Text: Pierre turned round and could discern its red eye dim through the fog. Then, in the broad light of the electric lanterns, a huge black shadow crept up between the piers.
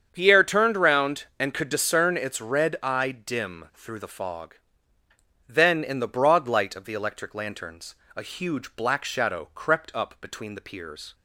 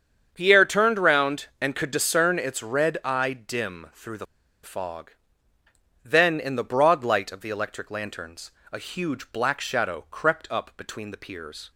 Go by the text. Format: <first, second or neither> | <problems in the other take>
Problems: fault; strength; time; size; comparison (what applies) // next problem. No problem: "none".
first | starts louder than the rest; strong; until 1.3 s; 7.5 dB; strong in the first // pauses between "the" and "fog"; at 4.2 s; 0.39 s long